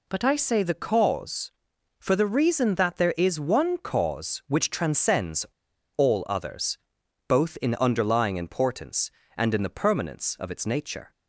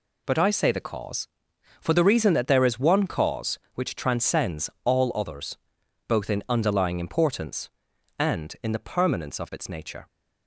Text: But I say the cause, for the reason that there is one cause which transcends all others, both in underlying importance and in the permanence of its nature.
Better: second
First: pauses between "transcends" and "all"; noticeable; at 5.4 s; 0.51 s long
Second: none

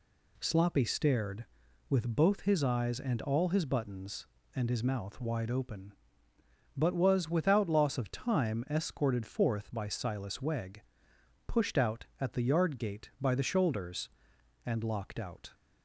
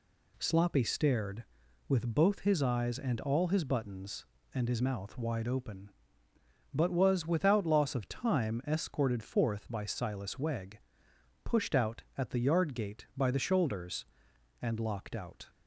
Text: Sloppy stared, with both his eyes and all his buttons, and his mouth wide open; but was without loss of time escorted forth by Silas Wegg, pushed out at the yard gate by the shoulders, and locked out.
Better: neither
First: none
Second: none

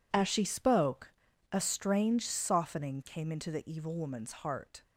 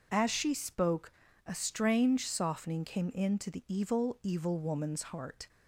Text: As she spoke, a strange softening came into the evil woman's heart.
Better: first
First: none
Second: says "evil" twice; at 4.2 s

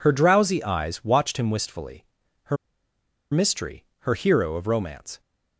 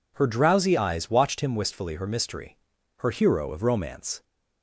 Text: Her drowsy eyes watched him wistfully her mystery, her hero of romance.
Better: second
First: pauses between "wistfully" and "her"; at 2.0 s; 0.40 s long // pauses between "her" and "mystery"; noticeable; at 2.5 s; 0.75 s long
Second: none

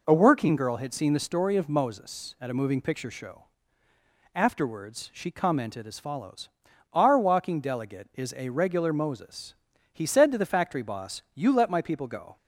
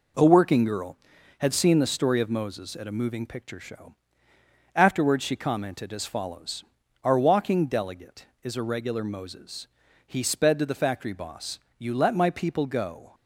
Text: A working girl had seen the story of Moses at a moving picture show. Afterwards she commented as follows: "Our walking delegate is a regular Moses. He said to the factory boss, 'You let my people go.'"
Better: first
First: none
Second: says "sped" for "said"; at 10.2 s

